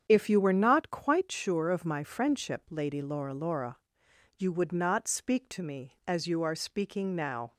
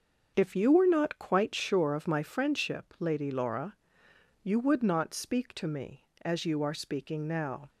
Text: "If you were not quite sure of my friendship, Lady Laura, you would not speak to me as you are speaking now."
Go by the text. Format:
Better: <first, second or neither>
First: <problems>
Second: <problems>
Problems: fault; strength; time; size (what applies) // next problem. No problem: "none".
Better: second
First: starts louder than the rest; strong; until 1.0 s; 8 dB // says "Laura" twice; at 3.3 s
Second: starts louder than the rest; until 1.3 s; 6.5 dB